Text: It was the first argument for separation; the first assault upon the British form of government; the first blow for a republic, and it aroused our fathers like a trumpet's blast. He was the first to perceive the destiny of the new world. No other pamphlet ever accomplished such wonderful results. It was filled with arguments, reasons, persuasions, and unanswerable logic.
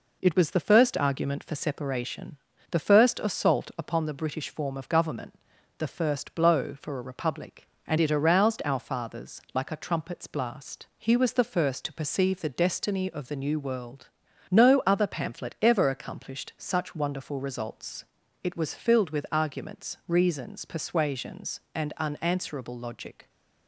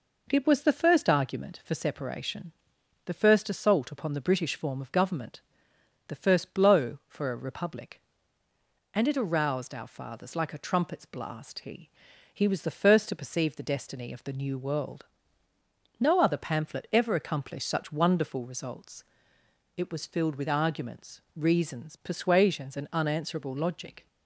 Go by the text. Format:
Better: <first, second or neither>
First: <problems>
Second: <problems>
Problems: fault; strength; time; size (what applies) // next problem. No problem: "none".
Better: first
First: none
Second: says "He" twice; at 12.3 s